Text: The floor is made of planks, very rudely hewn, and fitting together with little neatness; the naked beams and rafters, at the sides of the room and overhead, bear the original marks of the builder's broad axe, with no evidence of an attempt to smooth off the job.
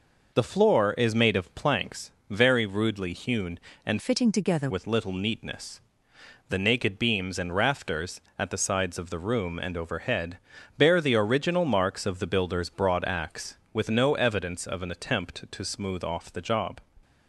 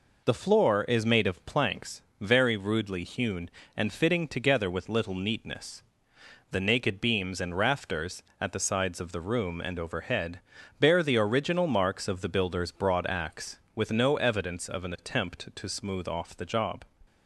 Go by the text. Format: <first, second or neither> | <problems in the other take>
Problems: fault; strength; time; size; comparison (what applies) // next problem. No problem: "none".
second | changes voice from "fitting" to "together"; from 3.9 to 4.7 s; 0.8 s long